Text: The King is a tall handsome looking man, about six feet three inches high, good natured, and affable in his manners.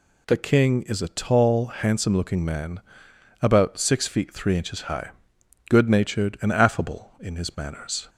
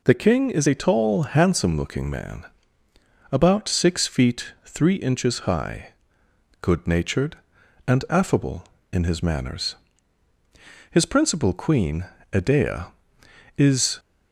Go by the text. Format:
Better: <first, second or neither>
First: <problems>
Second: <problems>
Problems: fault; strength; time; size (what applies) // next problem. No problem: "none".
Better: first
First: none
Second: goes on to say "His principal queen Edea is"; strong; from 10.8 s on; 3.1 s long